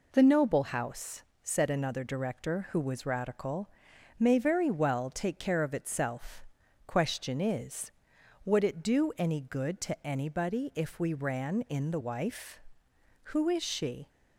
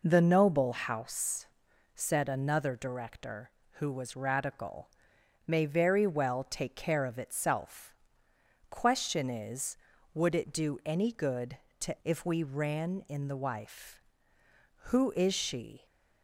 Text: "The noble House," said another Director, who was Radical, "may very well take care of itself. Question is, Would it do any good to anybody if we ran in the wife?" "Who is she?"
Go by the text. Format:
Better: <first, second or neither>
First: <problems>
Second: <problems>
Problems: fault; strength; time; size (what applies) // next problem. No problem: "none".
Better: first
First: none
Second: skips "anybody"; at 12.0 s